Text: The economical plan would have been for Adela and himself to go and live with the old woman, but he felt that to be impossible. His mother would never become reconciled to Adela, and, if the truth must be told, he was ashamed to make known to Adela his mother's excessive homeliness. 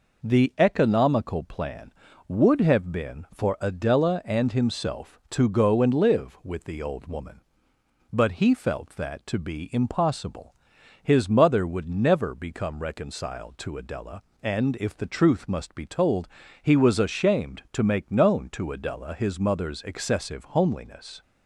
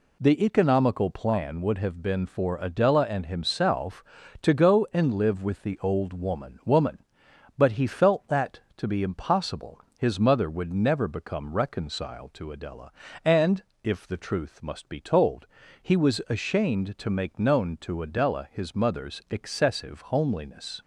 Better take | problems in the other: first | says "woman" twice; at 6.6 s

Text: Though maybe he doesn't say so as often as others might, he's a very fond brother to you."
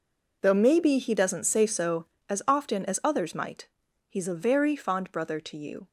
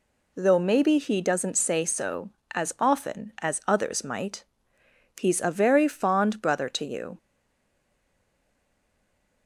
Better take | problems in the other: first | stays silent after the last word; from 7.1 s on; 2.3 s long

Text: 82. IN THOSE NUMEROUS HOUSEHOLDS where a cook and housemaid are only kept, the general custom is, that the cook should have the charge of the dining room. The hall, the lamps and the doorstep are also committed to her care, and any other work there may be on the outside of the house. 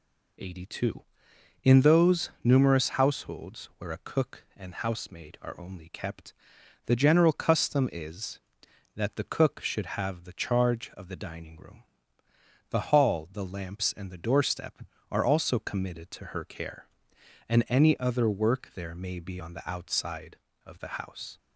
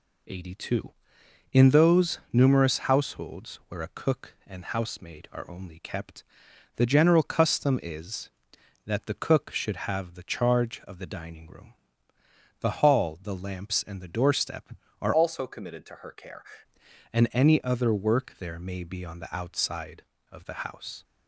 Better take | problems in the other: first | changes voice from "also" to "care"; from 15.1 to 16.4 s; 1.3 s long

